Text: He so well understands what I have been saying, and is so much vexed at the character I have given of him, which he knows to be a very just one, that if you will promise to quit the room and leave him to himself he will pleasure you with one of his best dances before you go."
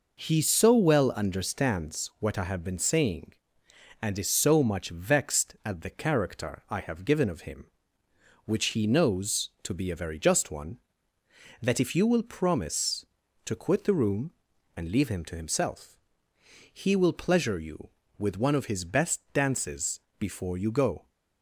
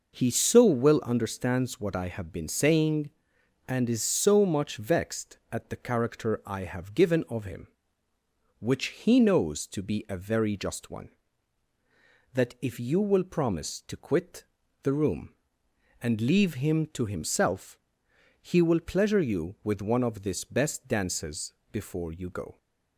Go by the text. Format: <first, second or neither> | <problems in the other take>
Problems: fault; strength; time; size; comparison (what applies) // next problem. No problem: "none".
first | pauses between "quit" and "the"; at 14.4 s; 0.40 s long // pauses between "himself" and "he"; noticeable; at 17.7 s; 0.66 s long; noticeable in the first // says "this" for "his"; at 20.2 s // pauses between "dances" and "before"; slight; at 21.5 s; 0.18 s long; slight in the first